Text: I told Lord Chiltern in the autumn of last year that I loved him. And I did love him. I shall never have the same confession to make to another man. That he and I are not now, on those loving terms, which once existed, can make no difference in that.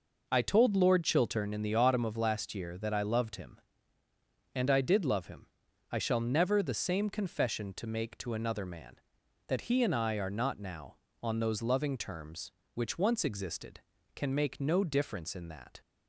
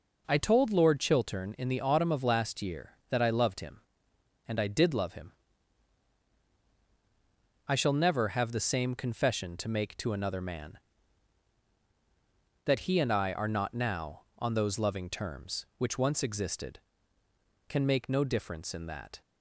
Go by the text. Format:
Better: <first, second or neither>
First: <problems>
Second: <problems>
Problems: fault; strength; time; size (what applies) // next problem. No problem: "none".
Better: second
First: skips "have"; at 6.6 s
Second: none